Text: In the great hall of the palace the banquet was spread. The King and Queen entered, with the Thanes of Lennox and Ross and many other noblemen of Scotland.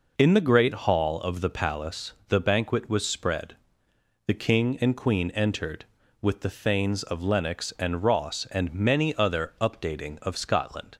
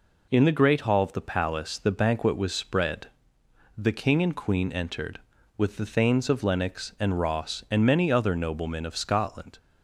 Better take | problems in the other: second | pauses between "palace" and "the"; slight; at 2.1 s; 0.16 s long // says "updating" for "noblemen"; at 9.5 s

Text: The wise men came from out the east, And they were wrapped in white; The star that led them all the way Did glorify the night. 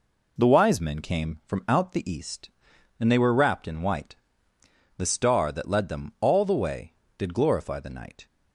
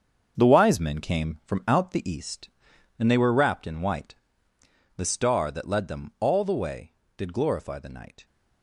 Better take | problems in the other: first | gets quieter; strong; throughout; 9 dB

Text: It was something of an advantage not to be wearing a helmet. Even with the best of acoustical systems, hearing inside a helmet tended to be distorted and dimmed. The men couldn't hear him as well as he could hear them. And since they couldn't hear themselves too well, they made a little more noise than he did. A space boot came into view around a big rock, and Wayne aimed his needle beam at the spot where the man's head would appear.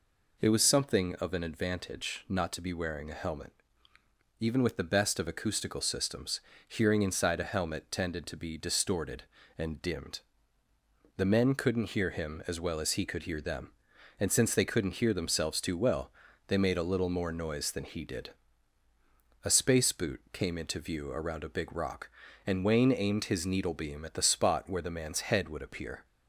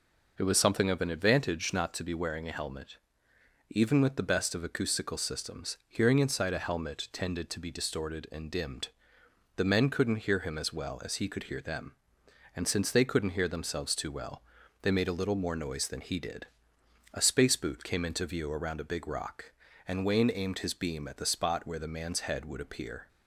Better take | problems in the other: first | skips "needle"; at 20.7 s

